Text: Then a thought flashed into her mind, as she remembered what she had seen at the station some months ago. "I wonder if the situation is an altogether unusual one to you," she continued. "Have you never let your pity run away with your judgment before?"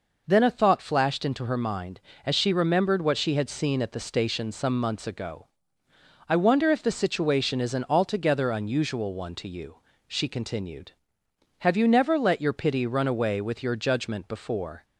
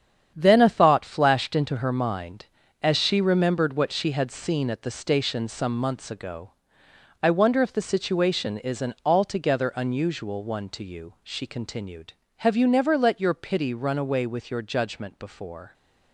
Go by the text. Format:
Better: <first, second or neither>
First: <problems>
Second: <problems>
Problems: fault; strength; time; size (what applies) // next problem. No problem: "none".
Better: first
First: none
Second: gets quieter; strong; throughout; 8.5 dB